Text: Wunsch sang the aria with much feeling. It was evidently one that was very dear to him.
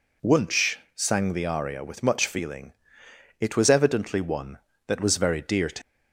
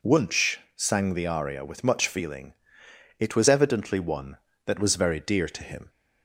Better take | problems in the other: second | pauses between "Wunsch" and "sang"; slight; at 0.7 s; 0.20 s long; slight in the second // stops before "him"; at 5.8 s

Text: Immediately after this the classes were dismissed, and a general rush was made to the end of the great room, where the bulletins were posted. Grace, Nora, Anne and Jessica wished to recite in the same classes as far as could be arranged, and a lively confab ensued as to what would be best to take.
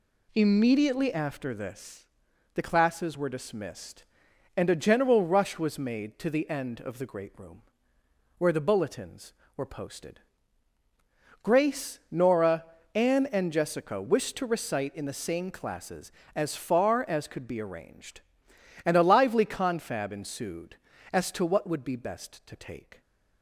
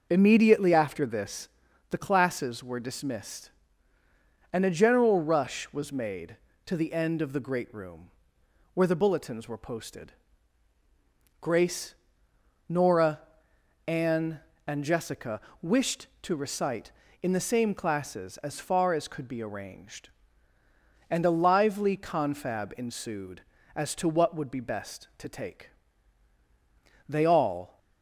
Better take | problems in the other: first | pauses between "this" and "the"; at 1.4 s; 0.42 s long; noticeable in the first // pauses between "Jessica" and "wished"; slight; at 15.3 s; 0.22 s long // goes on to say "They all"; noticeable; from 27.0 s on; 0.70 s long

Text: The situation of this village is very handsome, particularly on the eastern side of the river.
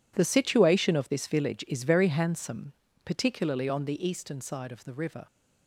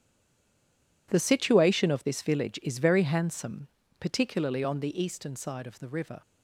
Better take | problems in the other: first | stays silent before the first word; until 1.0 s; 1.0 s long

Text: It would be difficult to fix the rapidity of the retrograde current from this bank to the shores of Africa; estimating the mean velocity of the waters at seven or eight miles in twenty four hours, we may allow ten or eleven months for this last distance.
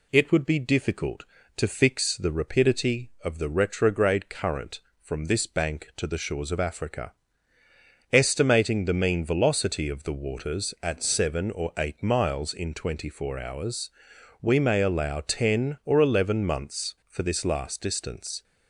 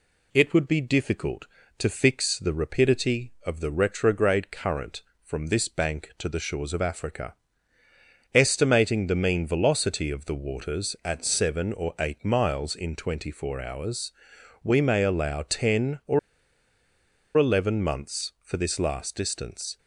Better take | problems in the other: first | pauses between "or" and "eleven"; at 16.1 s; 1.1 s long

